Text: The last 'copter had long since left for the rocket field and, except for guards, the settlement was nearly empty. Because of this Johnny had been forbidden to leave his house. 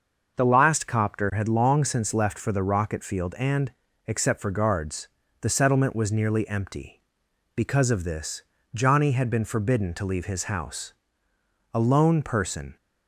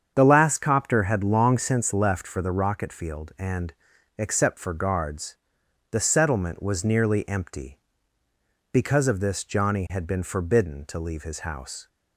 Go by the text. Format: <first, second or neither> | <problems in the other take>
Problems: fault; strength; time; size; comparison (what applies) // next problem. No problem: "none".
second | starts louder than the rest; until 1.3 s; 6.5 dB; strong in the second // pauses between "this" and "Johnny"; slight; at 8.4 s; 0.32 s long // goes on to say "A lone person"; noticeable; from 11.7 s on; 1.0 s long